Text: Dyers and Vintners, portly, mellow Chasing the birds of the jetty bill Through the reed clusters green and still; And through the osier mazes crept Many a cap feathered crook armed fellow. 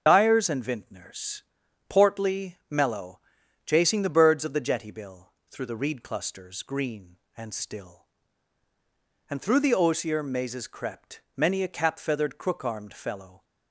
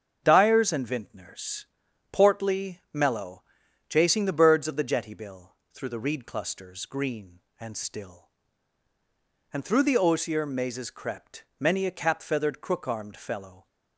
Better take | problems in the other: second | loses the start of "Dyers"; at 0.0 s; 45 ms // starts louder than the rest; until 1.0 s; 6.5 dB; also in the second // pauses between "mellow" and "Chasing"; noticeable; at 3.1 s; 0.46 s long; noticeable in the second // pauses between "bill" and "Through"; slight; at 5.3 s; 0.18 s long; slight in the second

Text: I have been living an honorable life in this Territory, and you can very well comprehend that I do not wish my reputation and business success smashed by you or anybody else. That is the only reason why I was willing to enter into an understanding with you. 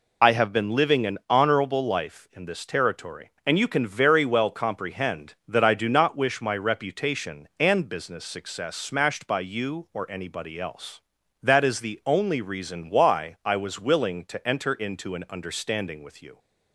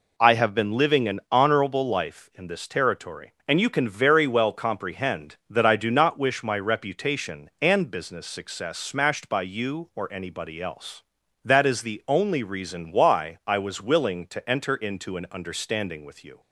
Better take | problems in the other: second | loses the start of "I"; at 0.2 s; 50 ms

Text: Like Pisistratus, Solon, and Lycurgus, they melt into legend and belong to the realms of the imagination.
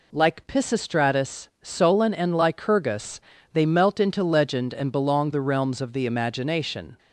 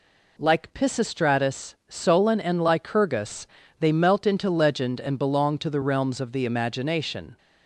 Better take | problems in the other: second | skips "to"; at 5.3 s

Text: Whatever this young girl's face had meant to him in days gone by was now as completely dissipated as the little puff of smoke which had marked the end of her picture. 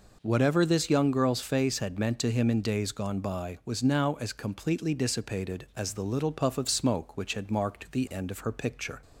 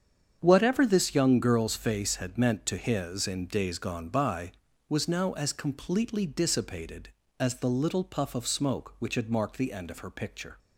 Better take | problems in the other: first | starts louder than the rest; strong; until 1.4 s; 7.5 dB // says "his" for "him"; at 2.7 s

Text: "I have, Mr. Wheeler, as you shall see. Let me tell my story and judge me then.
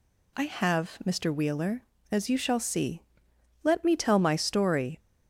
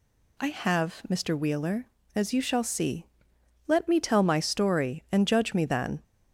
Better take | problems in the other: second | stops before "and judge me then"; at 4.9 s

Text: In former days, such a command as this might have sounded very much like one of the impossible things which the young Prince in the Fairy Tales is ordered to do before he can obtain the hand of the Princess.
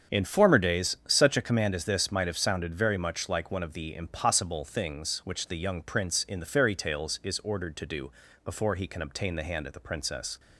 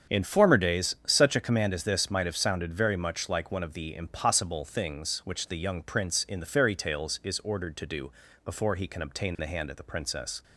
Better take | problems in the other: neither | starts louder than the rest; strong; the same in both // pauses between "do" and "before"; slight; the same in both

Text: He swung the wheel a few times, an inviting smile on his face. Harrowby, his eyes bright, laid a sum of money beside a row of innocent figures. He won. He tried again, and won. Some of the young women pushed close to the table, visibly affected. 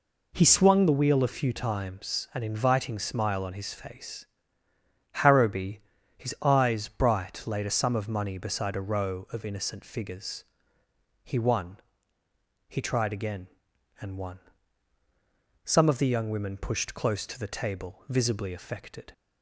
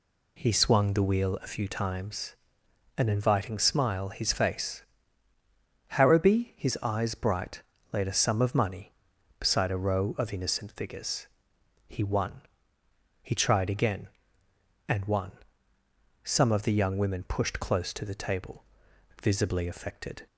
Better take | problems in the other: first | skips "on"; at 4.0 s

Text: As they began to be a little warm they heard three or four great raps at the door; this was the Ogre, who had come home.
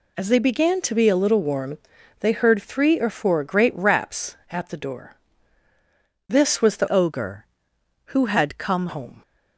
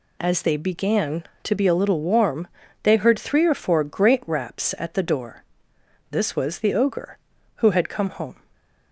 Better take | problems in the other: second | pauses between "warm" and "they"; at 1.7 s; 0.42 s long; slight in the second // changes voice from "Ogre" to "come"; from 6.8 to 8.8 s; 2.0 s long

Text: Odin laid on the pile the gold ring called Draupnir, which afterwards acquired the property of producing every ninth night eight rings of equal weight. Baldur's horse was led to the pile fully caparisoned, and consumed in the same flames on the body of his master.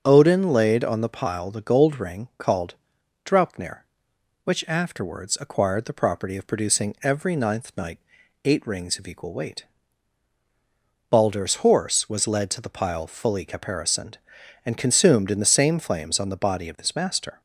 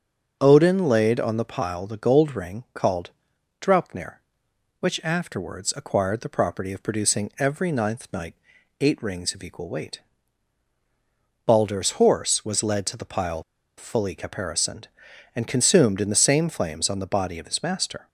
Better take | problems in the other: first | starts louder than the rest; until 1.4 s; 6.5 dB; also in the first // pauses between "called" and "Draupnir"; noticeable; at 3.1 s; 0.50 s long; noticeable in the first // pauses between "night" and "eight"; noticeable; at 8.3 s; 0.46 s long; noticeable in the first // pauses between "pile" and "fully"; slight; at 13.4 s; 0.34 s long

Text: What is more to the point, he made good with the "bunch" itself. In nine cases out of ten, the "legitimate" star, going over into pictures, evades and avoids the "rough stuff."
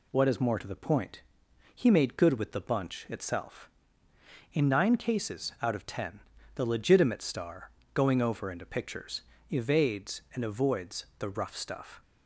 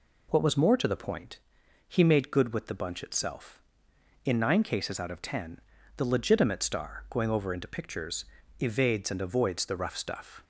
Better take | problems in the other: first | says "was" for "is"; at 0.4 s

